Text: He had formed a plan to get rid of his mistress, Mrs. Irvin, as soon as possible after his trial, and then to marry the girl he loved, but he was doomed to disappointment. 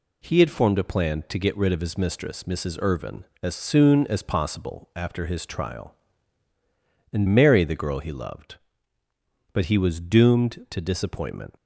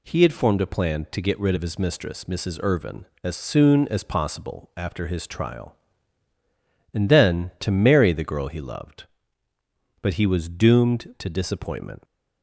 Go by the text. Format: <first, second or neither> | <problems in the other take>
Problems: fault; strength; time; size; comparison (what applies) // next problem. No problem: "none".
second | skips "then to"; at 7.2 s